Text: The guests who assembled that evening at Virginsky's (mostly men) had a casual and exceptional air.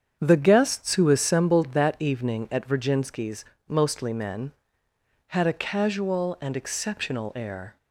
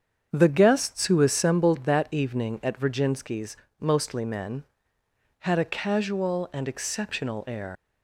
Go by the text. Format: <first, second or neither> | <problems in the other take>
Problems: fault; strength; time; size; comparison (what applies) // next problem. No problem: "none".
first | starts louder than the rest; strong; until 1.3 s; 7.5 dB; strong in the first // leaves "air" unfinished; at 7.7 s; 130 ms